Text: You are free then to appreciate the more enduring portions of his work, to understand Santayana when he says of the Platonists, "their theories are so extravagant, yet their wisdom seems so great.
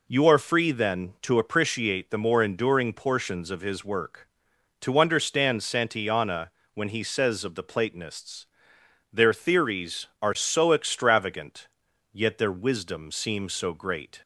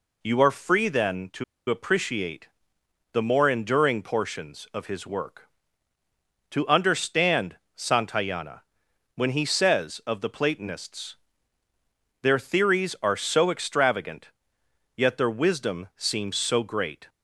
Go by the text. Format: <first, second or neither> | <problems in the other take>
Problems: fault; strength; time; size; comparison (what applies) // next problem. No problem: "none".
first | pauses between "to" and "appreciate"; slight; at 1.4 s; 0.25 s long // pauses between "appreciate" and "the"; noticeable; at 2.4 s; 0.66 s long // pauses between "understand" and "Santayana"; slight; at 7.5 s; 0.20 s long // pauses between "Santayana" and "when"; noticeable; at 8.6 s; 0.54 s long; slight in the first